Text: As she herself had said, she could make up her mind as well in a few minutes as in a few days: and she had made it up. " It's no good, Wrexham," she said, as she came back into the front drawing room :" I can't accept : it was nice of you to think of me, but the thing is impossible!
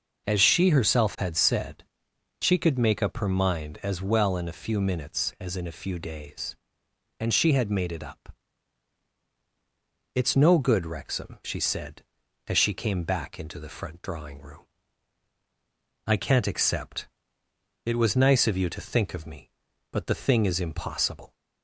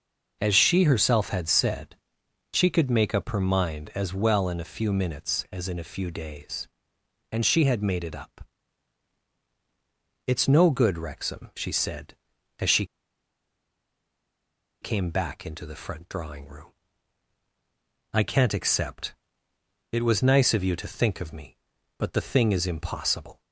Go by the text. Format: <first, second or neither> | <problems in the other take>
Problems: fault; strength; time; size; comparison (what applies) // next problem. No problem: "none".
first | starts louder than the rest; until 1.4 s; 6.5 dB; also in the first // pauses between "she" and "came"; strong; at 12.8 s; 1.9 s long